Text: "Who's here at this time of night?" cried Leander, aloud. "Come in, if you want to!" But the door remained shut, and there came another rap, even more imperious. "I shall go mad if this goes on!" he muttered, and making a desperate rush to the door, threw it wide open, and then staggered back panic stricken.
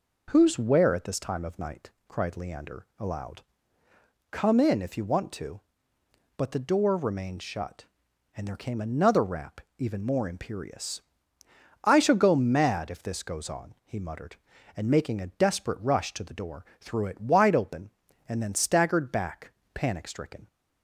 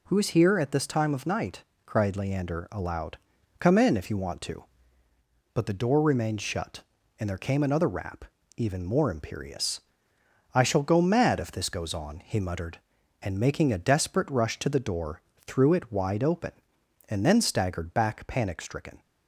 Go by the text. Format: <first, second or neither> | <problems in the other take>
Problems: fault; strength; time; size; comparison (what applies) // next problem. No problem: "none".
second | says "where" for "here"; at 0.5 s // pauses between "back" and "panic"; slight; at 19.4 s; 0.24 s long